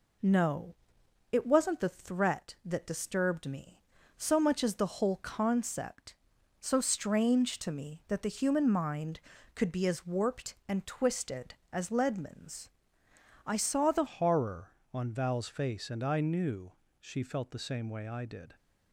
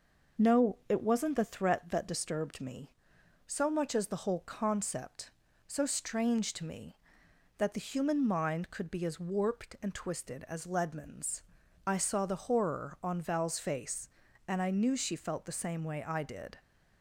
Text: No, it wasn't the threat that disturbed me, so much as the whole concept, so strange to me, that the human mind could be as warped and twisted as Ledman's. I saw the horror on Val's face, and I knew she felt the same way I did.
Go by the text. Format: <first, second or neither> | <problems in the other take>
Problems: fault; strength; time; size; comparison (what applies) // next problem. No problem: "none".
second | changes voice at "horror"; from 14.0 s on; 4.5 s long // pauses between "knew" and "she"; slight; at 16.7 s; 0.26 s long